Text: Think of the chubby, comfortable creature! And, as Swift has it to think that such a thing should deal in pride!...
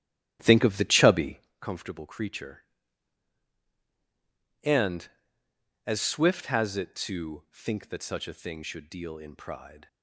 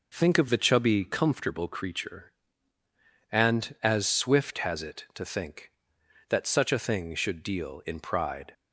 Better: second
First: starts louder than the rest; strong; until 1.5 s; 13 dB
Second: none

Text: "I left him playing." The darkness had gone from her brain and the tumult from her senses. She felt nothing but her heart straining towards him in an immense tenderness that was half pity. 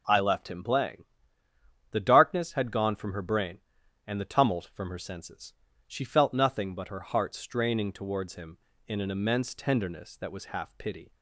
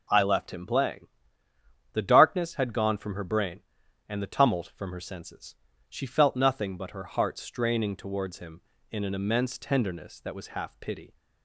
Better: neither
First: none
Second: none

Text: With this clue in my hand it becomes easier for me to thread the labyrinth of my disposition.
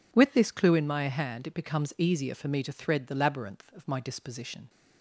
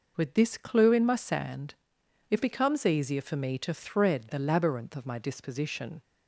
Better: first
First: none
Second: says "sand" for "hand"; at 1.1 s

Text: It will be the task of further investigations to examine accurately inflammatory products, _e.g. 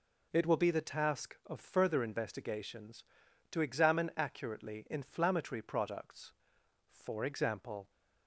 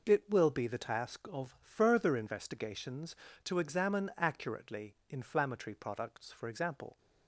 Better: neither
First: none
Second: none

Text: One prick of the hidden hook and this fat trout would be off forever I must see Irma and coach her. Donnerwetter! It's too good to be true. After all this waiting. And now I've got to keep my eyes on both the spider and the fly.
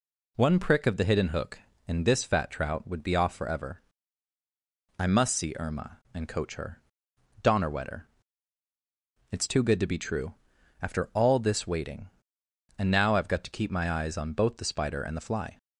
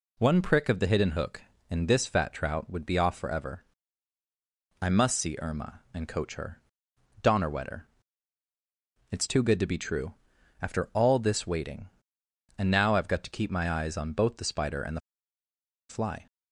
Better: first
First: pauses between "forever" and "I"; at 3.8 s; 1.1 s long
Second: pauses between "forever" and "I"; at 3.6 s; 1.1 s long // pauses between "the" and "fly"; noticeable; at 15.0 s; 0.89 s long

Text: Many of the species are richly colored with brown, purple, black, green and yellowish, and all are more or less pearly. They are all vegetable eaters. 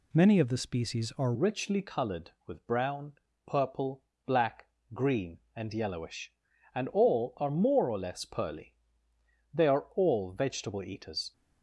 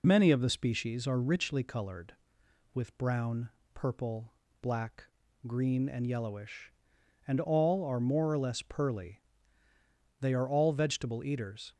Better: second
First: changes voice at "richly"; from 1.3 s on; 10.0 s long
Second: none

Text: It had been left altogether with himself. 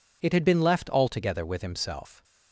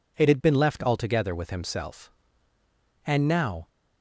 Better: first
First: none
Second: goes on to say "And now"; noticeable; from 3.0 s on; 0.62 s long

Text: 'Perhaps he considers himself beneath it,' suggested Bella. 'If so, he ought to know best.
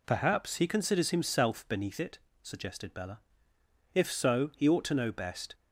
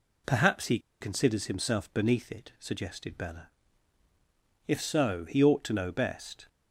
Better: first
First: none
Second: pauses between "he" and "considers"; slight; at 0.7 s; 0.22 s long

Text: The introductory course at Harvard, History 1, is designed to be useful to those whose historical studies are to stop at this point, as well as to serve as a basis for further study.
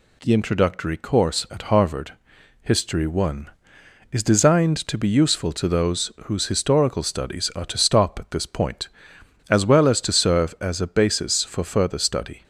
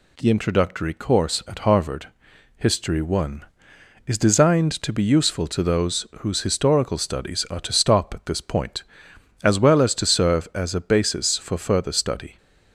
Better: neither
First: none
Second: none

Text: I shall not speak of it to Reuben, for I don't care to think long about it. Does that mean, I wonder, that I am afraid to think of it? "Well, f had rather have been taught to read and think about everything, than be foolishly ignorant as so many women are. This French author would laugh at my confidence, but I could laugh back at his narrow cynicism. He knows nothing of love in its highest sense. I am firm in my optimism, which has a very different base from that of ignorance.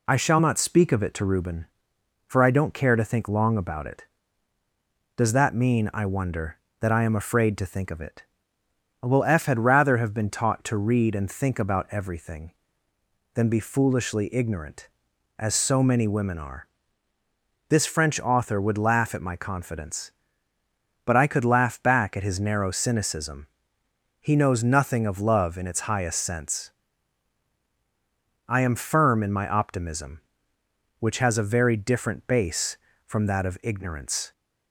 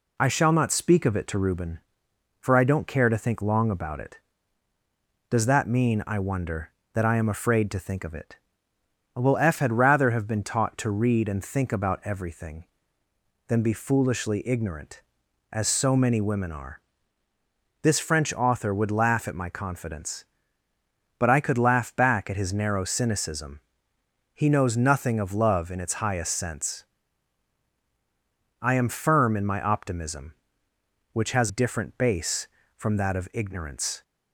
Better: first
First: none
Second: skips "a very"; at 31.4 s

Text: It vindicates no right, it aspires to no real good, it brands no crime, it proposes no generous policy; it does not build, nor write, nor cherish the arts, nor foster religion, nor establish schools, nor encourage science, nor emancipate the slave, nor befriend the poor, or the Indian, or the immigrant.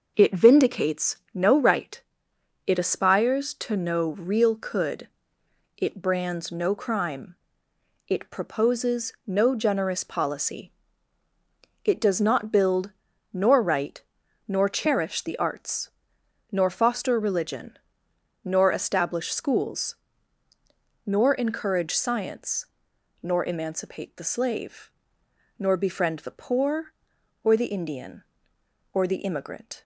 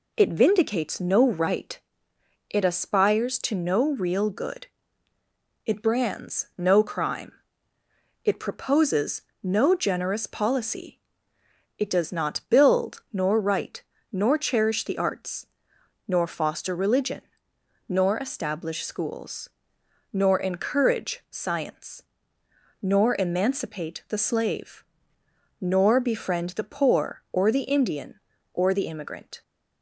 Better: second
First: pauses between "vindicates" and "no"; slight; at 1.1 s; 0.16 s long // says "could" for "good"; at 4.5 s // pauses between "proposes" and "no"; slight; at 9.1 s; 0.16 s long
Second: pauses between "proposes" and "no"; slight; at 9.2 s; 0.20 s long

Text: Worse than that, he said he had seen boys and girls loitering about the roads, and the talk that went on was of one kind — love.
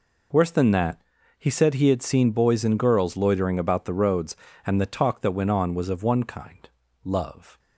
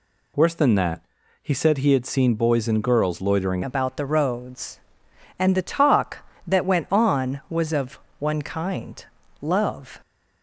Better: first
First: none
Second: changes voice at "about"; from 3.6 s on; 6.4 s long // pauses between "of" and "one"; slight; at 7.9 s; 0.20 s long

